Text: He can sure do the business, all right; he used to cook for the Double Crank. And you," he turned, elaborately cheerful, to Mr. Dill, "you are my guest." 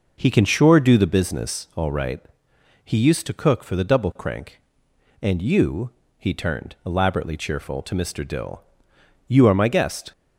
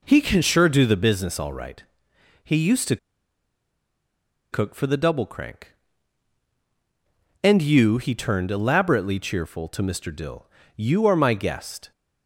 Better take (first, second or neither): first